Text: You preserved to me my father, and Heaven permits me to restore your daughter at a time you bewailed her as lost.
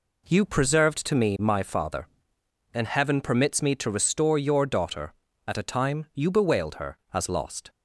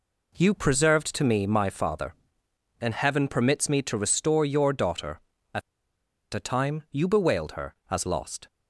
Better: first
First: none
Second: pauses between "at" and "a"; noticeable; at 5.6 s; 0.73 s long

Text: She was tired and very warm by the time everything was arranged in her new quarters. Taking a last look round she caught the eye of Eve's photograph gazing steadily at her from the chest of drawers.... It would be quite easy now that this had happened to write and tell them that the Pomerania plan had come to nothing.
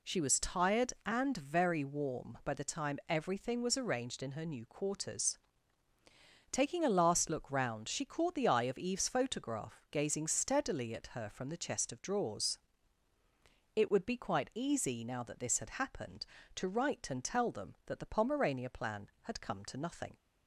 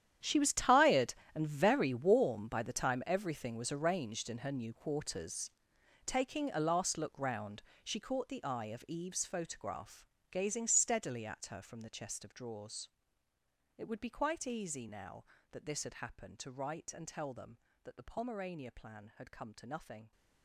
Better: first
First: none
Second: gets quieter; strong; throughout; 16.5 dB // pauses between "round" and "she"; slight; at 7.6 s; 0.20 s long // pauses between "photograph" and "gazing"; slight; at 10.0 s; 0.24 s long

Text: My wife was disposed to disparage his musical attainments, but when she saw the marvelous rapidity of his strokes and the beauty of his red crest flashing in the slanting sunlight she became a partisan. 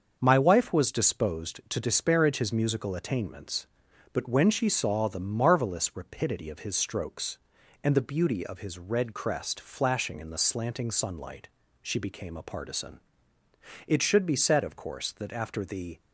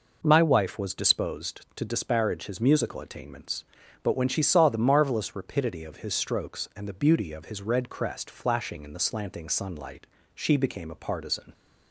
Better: second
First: starts louder than the rest; until 1.2 s; 6.5 dB // pauses between "sunlight" and "she"; slight; at 11.4 s; 0.36 s long // goes on to say "It should be said of course that after the"; strong; from 13.8 s on; 2.1 s long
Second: pauses between "sunlight" and "she"; slight; at 10.0 s; 0.30 s long

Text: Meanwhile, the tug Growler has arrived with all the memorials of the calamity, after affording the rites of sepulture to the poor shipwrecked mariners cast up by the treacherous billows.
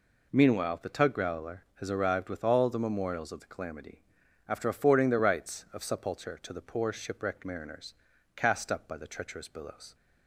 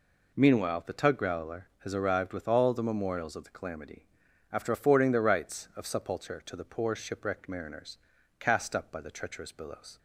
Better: neither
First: pauses between "mariners" and "cast"; at 7.9 s; 0.40 s long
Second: pauses between "mariners" and "cast"; at 7.9 s; 0.40 s long

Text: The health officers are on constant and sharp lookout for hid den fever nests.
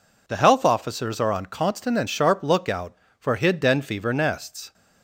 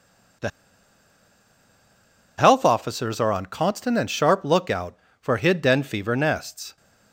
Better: first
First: none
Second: pauses between "The" and "health"; strong; at 0.4 s; 1.8 s long

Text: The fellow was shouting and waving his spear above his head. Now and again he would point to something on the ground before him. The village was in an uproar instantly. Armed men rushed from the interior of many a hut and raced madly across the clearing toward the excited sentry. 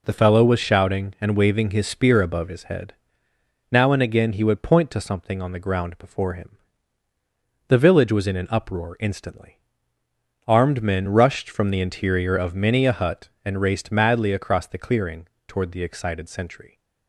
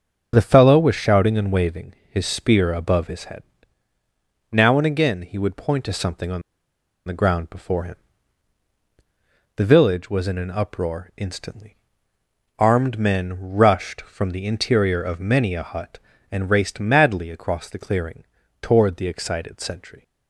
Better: first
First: pauses between "clearing" and "toward"; slight; at 15.2 s; 0.22 s long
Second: starts louder than the rest; until 1.3 s; 6 dB // pauses between "waving" and "his"; slight; at 1.9 s; 0.16 s long // pauses between "on" and "the"; noticeable; at 6.4 s; 0.64 s long // pauses between "clearing" and "toward"; slight; at 18.2 s; 0.36 s long

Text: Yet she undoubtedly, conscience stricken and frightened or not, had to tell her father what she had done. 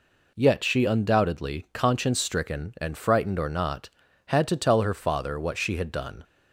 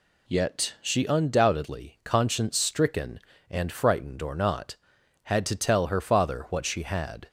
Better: first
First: none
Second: stops before "done"; at 7.2 s

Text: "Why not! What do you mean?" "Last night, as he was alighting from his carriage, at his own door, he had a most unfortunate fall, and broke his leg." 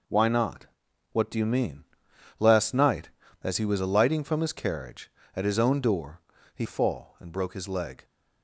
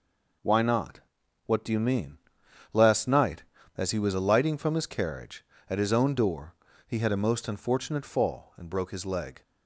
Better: second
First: skips "had a most unfortunate"; at 6.6 s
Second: none

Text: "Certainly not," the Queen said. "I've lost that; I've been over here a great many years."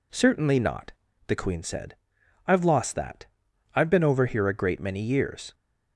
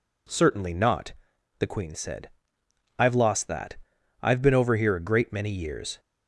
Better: neither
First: none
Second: none

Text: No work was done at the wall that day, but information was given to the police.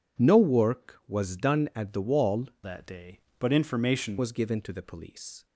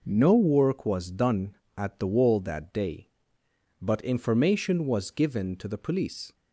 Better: second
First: changes voice from "that" to "information"; from 2.6 to 4.1 s; 1.5 s long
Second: none

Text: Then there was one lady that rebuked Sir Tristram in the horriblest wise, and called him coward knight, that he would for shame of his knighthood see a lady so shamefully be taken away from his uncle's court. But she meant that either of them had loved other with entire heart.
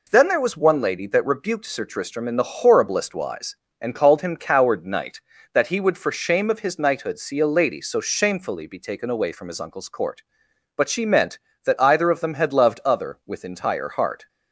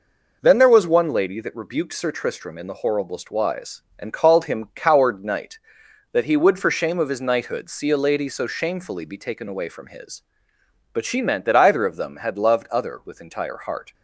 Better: first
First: none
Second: skips "uncle's court"; at 10.5 s

